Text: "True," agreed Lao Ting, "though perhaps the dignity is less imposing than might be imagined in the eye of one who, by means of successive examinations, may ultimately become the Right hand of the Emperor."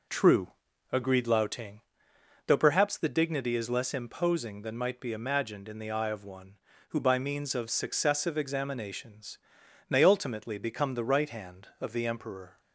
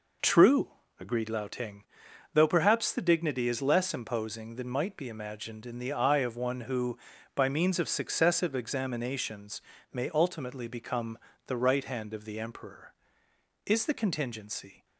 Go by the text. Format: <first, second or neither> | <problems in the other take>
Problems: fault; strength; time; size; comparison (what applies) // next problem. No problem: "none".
first | pauses between "become" and "the"; slight; at 11.1 s; 0.30 s long // goes on to say "Is the contingency"; noticeable; from 13.6 s on; 1.2 s long